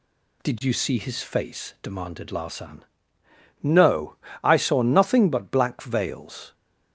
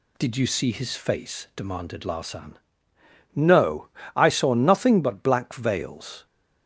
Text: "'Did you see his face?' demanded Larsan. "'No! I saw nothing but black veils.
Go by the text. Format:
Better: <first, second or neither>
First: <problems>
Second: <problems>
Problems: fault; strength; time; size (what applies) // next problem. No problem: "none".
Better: neither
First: none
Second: none